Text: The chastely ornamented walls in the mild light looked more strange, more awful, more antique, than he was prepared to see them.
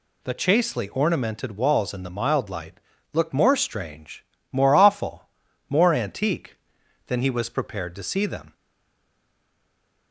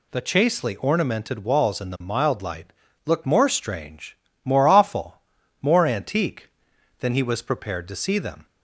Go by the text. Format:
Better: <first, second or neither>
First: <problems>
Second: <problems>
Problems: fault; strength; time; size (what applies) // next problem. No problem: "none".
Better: second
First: pauses between "light" and "looked"; slight; at 2.7 s; 0.34 s long // stays silent after the last word; noticeable; from 8.5 s on; 1.6 s long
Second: pauses between "light" and "looked"; slight; at 2.7 s; 0.34 s long